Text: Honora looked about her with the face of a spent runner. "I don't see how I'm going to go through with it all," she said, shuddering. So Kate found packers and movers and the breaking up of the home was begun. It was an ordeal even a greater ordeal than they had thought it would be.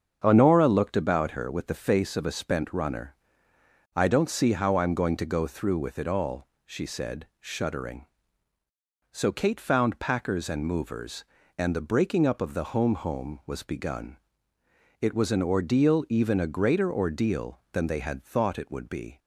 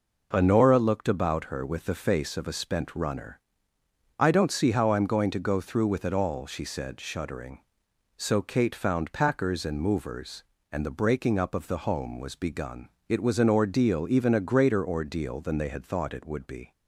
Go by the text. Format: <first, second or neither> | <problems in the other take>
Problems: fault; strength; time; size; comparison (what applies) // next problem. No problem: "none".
second | starts louder than the rest; strong; until 1.2 s; 7.5 dB // says "home" twice; at 12.9 s